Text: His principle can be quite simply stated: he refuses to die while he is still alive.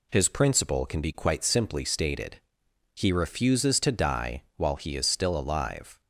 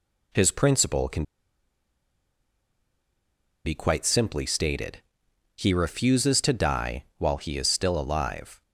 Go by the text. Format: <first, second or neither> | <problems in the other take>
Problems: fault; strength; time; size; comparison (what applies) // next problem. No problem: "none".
first | pauses between "can" and "be"; strong; at 1.2 s; 2.4 s long